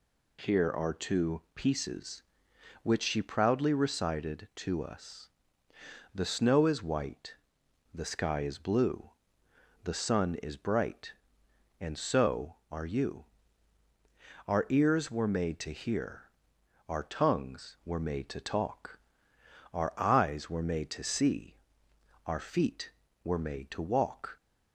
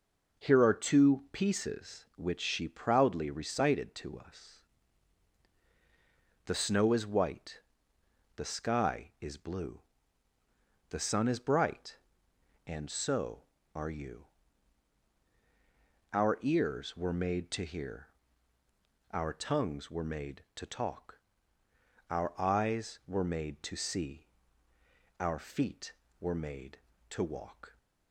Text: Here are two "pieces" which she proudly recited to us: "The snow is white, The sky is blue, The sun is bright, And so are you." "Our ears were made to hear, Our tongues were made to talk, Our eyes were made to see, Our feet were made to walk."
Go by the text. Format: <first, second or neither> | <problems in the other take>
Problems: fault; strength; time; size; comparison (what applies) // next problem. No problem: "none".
neither | none